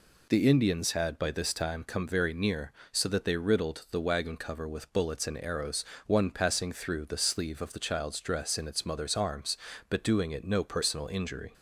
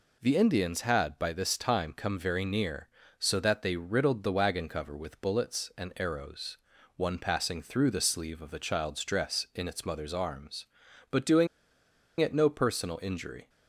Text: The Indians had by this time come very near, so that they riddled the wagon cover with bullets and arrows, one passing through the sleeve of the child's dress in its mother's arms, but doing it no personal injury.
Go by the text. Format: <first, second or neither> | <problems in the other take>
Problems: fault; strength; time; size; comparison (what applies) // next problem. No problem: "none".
first | pauses between "doing" and "it"; noticeable; at 11.4 s; 0.73 s long